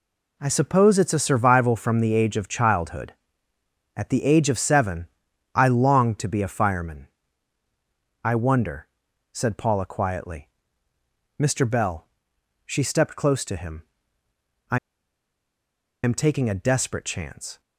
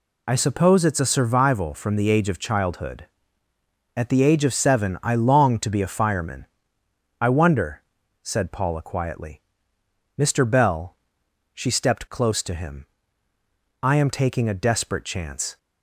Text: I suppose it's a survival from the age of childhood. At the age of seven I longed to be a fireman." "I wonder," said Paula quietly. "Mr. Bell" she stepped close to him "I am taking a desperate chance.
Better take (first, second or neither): second